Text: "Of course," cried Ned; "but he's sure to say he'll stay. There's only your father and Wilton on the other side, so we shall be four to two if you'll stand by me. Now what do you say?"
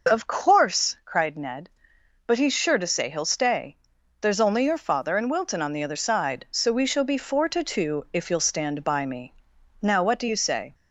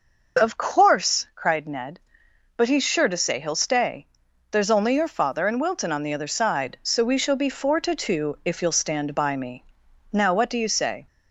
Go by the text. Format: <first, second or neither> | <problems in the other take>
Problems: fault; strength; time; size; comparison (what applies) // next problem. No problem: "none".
neither | none